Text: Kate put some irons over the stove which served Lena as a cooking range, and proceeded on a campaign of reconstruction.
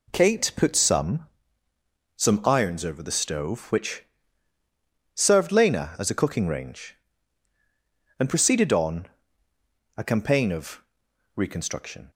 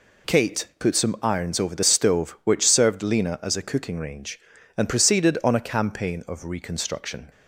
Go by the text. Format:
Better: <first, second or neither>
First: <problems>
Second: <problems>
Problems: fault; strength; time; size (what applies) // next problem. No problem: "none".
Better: second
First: says "some" twice; at 2.1 s // pauses between "which" and "served"; at 4.0 s; 1.1 s long // pauses between "on" and "a"; noticeable; at 9.0 s; 0.90 s long // pauses between "of" and "reconstruction"; noticeable; at 10.8 s; 0.54 s long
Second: none